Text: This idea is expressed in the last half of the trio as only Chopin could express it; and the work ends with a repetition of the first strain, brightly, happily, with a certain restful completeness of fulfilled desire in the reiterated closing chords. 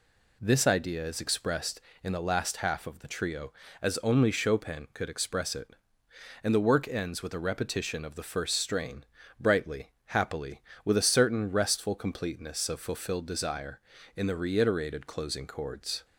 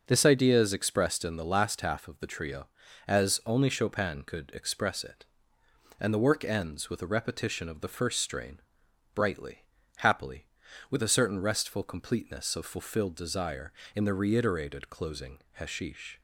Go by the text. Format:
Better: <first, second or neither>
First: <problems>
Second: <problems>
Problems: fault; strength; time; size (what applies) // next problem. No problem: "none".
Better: first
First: none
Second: says "hashish" for "chords"; at 15.5 s